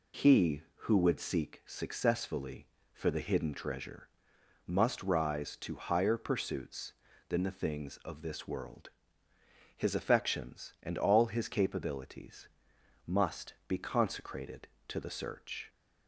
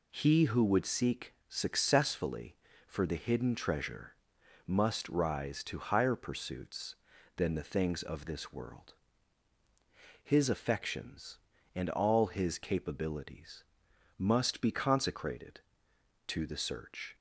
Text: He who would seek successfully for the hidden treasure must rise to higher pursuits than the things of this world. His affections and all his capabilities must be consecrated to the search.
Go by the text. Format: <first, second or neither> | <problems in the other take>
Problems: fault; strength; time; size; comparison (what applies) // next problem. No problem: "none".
neither | pauses between "treasure" and "must"; noticeable; the same in both // pauses between "capabilities" and "must"; noticeable; the same in both